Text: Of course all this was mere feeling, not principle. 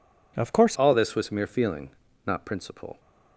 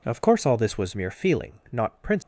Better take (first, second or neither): second